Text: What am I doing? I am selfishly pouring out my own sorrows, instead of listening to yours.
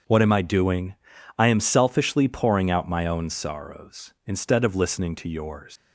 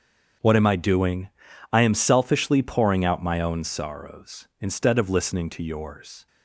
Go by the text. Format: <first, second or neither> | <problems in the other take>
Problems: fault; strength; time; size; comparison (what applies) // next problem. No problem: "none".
second | starts louder than the rest; until 1.4 s; 7 dB; strong in the second // leaves "yours" unfinished; at 5.7 s; 165 ms